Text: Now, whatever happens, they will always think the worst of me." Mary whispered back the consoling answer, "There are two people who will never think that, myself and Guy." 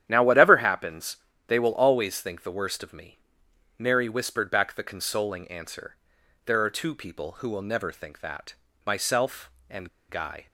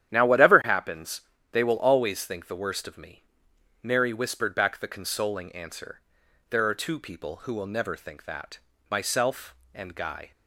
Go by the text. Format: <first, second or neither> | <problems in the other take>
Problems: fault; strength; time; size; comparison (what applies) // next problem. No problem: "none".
second | starts louder than the rest; strong; until 1.0 s; 10.5 dB; strong in the second // pauses between "and" and "Guy"; slight; at 9.8 s; 0.20 s long